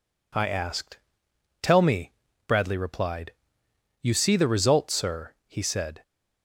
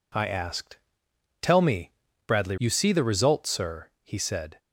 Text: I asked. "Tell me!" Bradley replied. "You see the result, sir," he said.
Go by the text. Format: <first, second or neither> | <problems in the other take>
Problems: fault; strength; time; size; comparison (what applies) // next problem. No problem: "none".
first | skips "replied"; at 2.5 s